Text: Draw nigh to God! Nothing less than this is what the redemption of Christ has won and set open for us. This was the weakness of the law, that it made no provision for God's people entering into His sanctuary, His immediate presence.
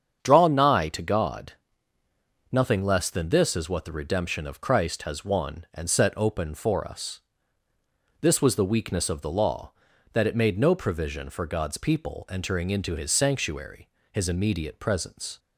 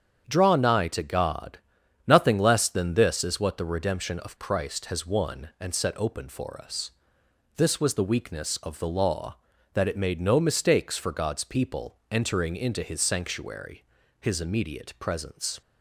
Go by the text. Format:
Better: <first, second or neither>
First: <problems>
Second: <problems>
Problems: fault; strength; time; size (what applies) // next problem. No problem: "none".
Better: first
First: starts louder than the rest; strong; until 1.2 s; 7.5 dB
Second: starts louder than the rest; strong; until 1.2 s; 7.5 dB // says "mistakes" for "provision"; at 10.4 s